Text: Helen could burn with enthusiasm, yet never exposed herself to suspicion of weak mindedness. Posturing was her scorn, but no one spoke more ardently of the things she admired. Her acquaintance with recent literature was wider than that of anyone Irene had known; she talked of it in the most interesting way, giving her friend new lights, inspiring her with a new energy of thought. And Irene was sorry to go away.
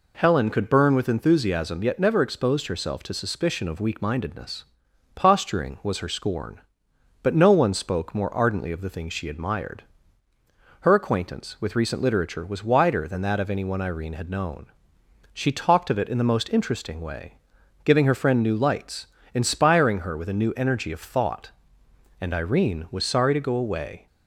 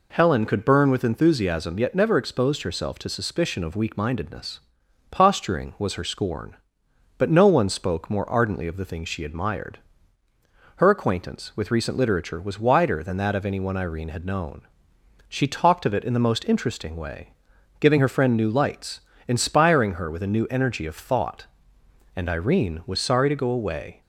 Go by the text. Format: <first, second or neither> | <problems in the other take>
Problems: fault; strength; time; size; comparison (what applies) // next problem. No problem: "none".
neither | none